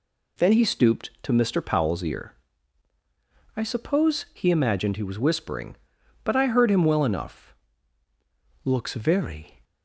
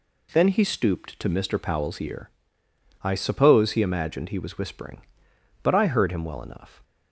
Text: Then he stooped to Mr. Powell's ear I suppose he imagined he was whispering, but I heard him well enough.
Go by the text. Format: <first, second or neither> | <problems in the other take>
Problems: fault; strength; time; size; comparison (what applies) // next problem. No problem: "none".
second | pauses between "ear" and "I"; at 2.3 s; 1.2 s long; noticeable in the second // goes on to say "Looks very"; noticeable; from 8.6 s on; 1.0 s long